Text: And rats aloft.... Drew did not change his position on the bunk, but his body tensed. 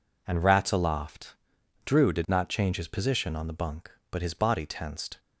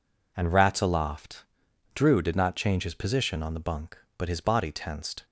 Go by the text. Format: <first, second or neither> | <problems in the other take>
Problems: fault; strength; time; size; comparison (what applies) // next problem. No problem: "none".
neither | none